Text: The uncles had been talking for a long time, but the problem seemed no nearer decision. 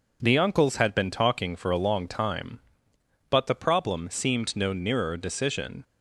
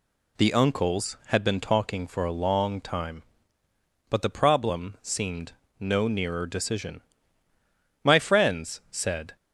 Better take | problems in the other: first | pauses between "seemed" and "no"; slight; at 5.5 s; 0.26 s long // goes on to say "My friends said"; from 8.0 s on; 1.3 s long

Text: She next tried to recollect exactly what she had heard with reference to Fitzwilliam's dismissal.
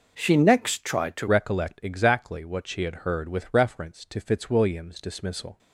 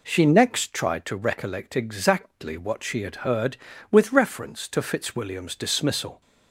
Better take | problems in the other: second | changes voice at "recollect"; from 1.2 s on; 4.3 s long

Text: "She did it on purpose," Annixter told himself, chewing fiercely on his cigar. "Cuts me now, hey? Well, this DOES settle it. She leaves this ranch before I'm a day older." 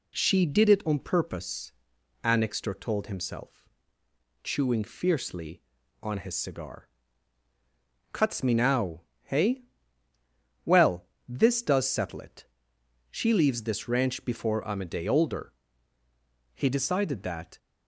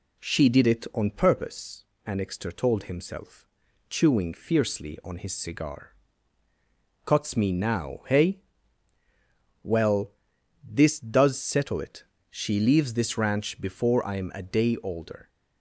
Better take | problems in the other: second | goes on to say "He decided that"; noticeable; from 16.5 s on; 1.0 s long

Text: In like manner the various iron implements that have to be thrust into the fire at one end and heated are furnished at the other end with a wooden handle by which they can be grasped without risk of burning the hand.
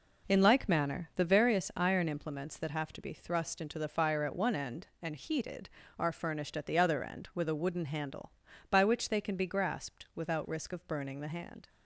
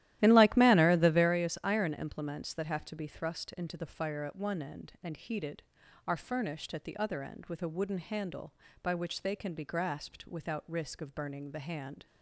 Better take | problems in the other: first | starts louder than the rest; strong; until 1.3 s; 14 dB

